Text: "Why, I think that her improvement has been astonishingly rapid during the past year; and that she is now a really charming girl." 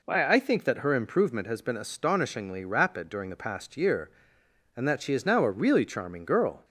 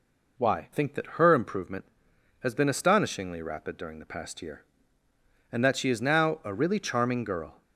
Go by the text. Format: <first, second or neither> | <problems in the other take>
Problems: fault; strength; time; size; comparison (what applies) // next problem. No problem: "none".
first | skips "I"; at 0.7 s